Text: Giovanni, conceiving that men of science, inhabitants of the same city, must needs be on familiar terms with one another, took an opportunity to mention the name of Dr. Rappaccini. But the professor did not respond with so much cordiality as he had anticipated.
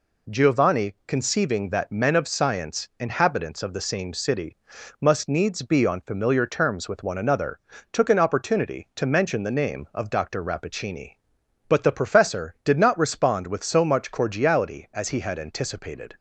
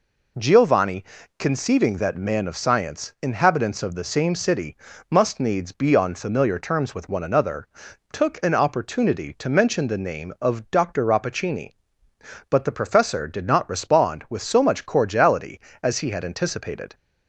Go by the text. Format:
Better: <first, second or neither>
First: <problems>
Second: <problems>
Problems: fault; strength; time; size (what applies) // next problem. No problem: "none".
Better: first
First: none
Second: says "man" for "men"; at 2.1 s